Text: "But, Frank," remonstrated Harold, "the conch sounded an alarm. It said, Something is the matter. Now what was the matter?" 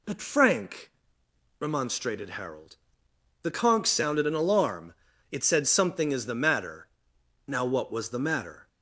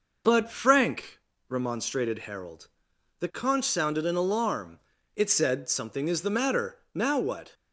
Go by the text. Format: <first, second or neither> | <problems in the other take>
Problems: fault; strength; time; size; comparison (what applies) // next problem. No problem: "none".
first | stops before "was the matter"; at 7.5 s